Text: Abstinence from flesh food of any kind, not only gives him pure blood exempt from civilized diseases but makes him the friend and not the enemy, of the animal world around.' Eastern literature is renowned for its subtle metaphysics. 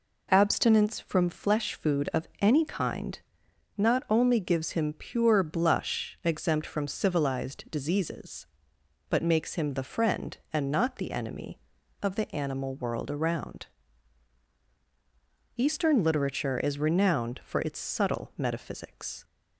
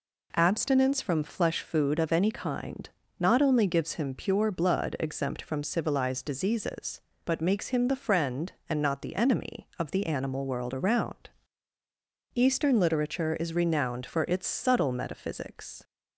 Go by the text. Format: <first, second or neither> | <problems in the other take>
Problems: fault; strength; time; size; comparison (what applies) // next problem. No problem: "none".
second | says "blush" for "blood"; at 5.4 s